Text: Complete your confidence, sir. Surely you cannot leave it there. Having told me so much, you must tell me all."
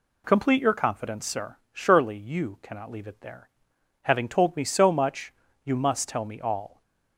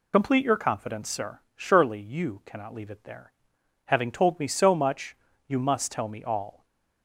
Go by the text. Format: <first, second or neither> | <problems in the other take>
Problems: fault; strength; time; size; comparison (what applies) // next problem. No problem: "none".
first | loses the start of "Complete"; at 0.1 s; 55 ms